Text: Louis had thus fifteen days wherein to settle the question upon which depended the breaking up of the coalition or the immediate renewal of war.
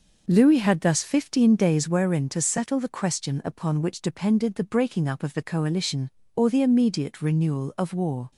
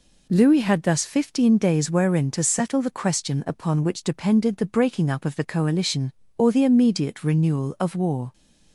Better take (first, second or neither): second